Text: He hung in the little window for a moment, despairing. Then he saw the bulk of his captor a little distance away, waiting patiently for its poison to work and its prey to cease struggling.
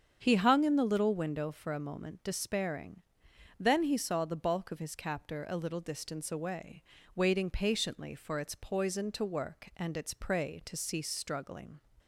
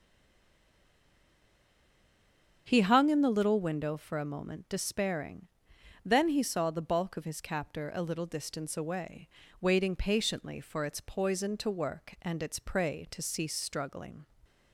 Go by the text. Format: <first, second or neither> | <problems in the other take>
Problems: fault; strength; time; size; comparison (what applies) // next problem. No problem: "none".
first | stays silent before the first word; strong; until 2.6 s; 2.6 s long // starts louder than the rest; strong; until 3.6 s; 7.5 dB; strong in the first